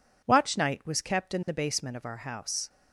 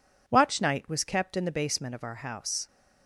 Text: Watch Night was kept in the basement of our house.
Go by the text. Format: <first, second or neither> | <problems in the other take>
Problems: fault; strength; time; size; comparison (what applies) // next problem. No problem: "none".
neither | none